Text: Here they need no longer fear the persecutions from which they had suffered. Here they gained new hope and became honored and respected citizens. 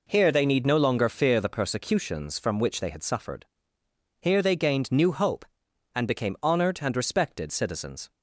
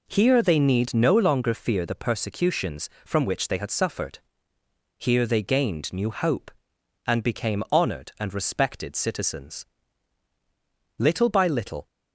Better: first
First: none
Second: goes on to say "Little by little"; noticeable; from 10.9 s on; 0.88 s long

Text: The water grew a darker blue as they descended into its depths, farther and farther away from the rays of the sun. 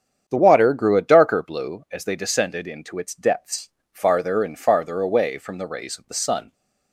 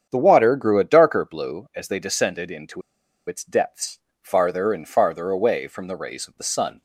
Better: first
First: starts louder than the rest; strong; until 1.3 s; 8 dB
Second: starts louder than the rest; strong; until 1.1 s; 8 dB // pauses between "into" and "its"; noticeable; at 2.8 s; 0.46 s long

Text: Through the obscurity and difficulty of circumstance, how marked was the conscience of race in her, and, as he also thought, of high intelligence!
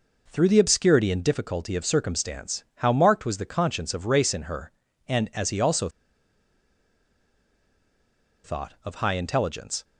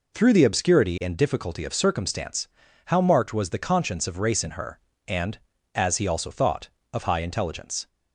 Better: second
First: pauses between "also" and "thought"; strong; at 5.8 s; 2.5 s long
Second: none

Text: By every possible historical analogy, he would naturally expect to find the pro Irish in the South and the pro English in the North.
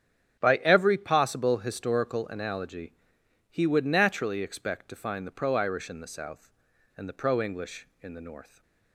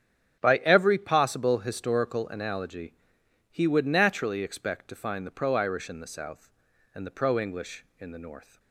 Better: neither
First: starts louder than the rest; strong; until 1.4 s; 9 dB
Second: starts louder than the rest; strong; until 1.4 s; 9 dB

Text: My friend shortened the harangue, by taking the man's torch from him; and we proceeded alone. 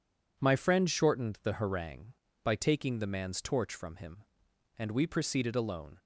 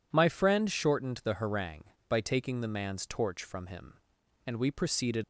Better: first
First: none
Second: stops before "alone"; at 5.2 s

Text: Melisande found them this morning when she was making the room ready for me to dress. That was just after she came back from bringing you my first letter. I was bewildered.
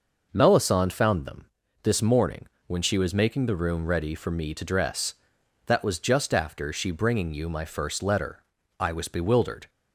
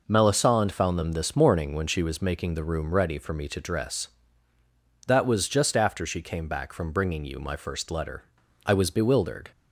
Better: second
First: pauses between "them" and "this"; slight; at 1.4 s; 0.36 s long // pauses between "morning" and "when"; slight; at 2.4 s; 0.20 s long // skips "came back from"; at 6.9 s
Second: none

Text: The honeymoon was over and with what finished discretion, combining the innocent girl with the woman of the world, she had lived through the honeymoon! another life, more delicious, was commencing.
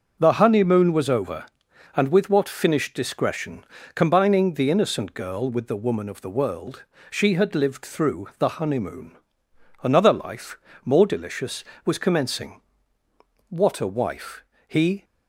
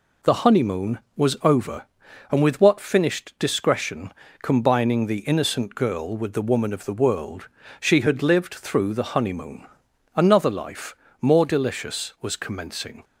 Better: second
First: goes on to say "What a wife he"; from 13.4 s on; 1.5 s long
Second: none

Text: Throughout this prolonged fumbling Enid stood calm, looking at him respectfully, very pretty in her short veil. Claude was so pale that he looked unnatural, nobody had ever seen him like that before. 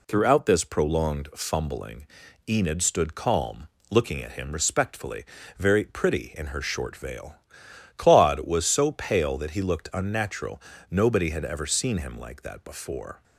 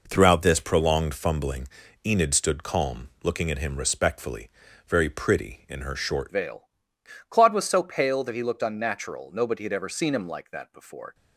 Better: first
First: pauses between "fumbling" and "Enid"; at 2.0 s; 0.40 s long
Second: pauses between "fumbling" and "Enid"; at 1.6 s; 0.38 s long // changes voice at "veil"; from 6.3 s on; 4.8 s long

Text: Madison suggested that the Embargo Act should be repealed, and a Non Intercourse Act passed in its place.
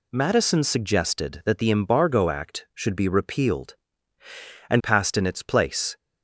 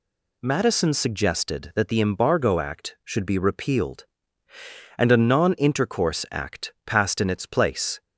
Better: second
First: skips "a Non Intercourse Act"; at 4.8 s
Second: none

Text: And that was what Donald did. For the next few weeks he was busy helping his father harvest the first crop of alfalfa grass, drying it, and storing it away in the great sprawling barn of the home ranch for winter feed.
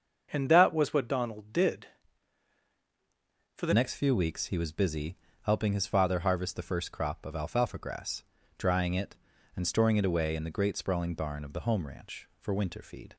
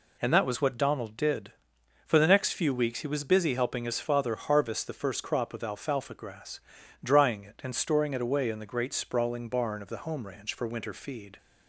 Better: second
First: starts louder than the rest; until 1.3 s; 6.5 dB // changes voice at "next"; from 3.7 s on; 9.4 s long // pauses between "busy" and "helping"; slight; at 5.1 s; 0.26 s long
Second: none

